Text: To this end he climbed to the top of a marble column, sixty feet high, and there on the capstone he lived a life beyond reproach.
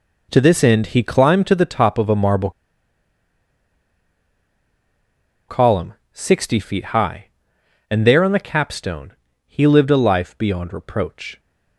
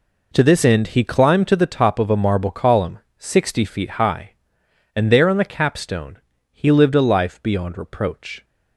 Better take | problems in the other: second | pauses between "marble" and "column"; strong; at 2.4 s; 2.9 s long // pauses between "capstone" and "he"; slight; at 9.1 s; 0.34 s long; slight in the second

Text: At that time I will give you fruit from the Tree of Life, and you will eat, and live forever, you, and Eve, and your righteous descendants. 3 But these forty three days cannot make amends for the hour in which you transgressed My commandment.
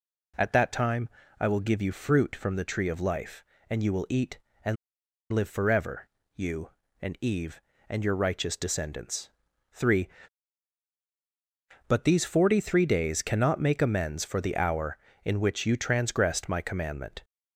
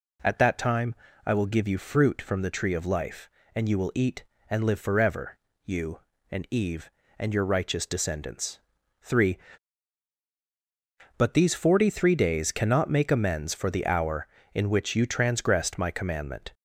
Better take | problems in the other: second | pauses between "time" and "I"; slight; at 1.0 s; 0.30 s long; slight in the second // pauses between "and" and "live"; noticeable; at 4.7 s; 0.57 s long

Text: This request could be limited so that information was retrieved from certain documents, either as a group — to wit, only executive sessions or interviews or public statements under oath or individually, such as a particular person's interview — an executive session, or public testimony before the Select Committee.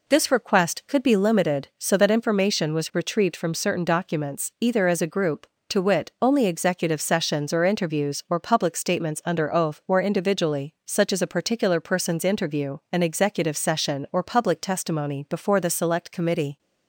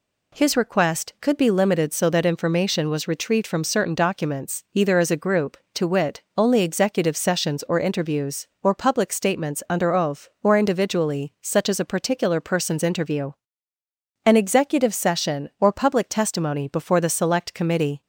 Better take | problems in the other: first | says "His" for "This"; at 0.3 s

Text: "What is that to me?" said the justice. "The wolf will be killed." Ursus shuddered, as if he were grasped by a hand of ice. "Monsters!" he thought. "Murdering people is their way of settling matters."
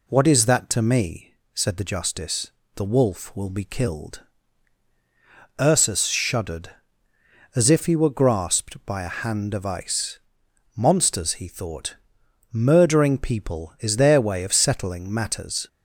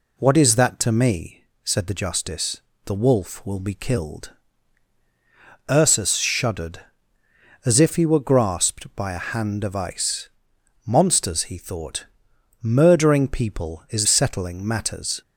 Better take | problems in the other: first | skips "their way of"; at 14.0 s

